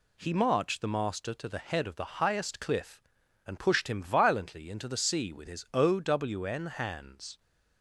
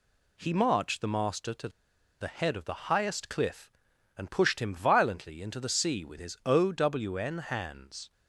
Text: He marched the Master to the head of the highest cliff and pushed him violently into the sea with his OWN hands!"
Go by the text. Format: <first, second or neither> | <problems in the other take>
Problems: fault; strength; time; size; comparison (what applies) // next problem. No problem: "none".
first | pauses between "to" and "the"; noticeable; at 1.6 s; 0.52 s long